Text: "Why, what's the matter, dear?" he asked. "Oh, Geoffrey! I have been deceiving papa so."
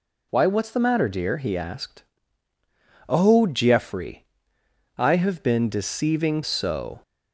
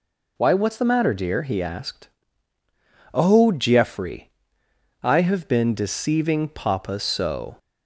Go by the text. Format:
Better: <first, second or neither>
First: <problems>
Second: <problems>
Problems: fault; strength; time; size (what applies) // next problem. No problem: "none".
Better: second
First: skips "papa"; at 6.4 s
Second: none